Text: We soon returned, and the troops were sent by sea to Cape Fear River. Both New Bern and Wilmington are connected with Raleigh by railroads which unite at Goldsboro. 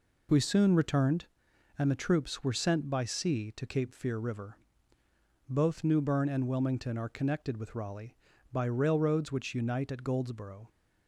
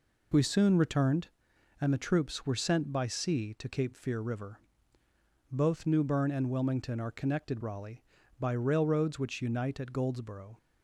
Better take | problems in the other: first | skips "with"; at 7.5 s

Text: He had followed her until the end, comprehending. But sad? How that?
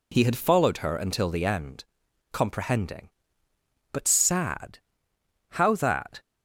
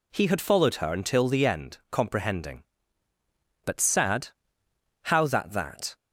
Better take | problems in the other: first | says "that" twice; at 5.5 s

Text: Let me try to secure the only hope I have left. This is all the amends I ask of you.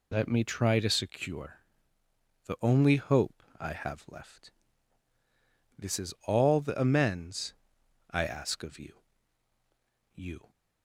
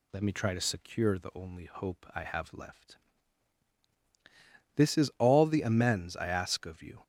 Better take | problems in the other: second | pauses between "secure" and "the"; noticeable; at 1.6 s; 0.84 s long // pauses between "hope" and "I"; slight; at 3.4 s; 0.18 s long // pauses between "amends" and "I"; noticeable; at 7.5 s; 0.57 s long // says "you" twice; at 10.1 s

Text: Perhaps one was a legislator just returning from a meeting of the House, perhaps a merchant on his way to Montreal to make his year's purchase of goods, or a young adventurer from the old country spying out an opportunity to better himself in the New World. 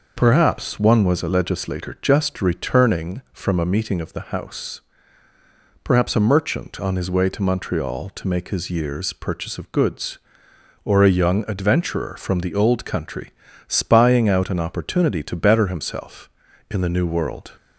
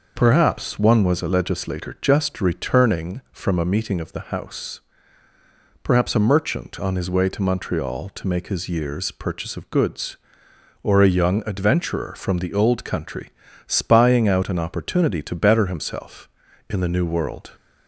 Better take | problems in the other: neither | pauses between "country" and "spying"; slight; the same in both

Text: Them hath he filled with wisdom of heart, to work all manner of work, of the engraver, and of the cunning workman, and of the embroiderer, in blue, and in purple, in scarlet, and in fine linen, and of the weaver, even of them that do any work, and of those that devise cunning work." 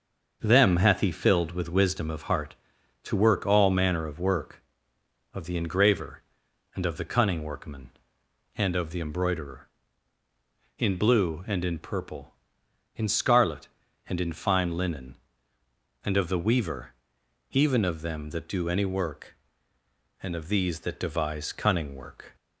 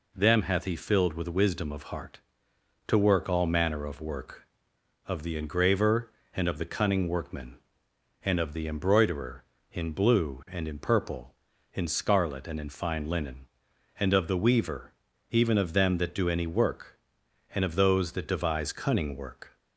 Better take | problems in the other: second | starts louder than the rest; until 1.4 s; 6.5 dB // says "these" for "those"; at 20.4 s

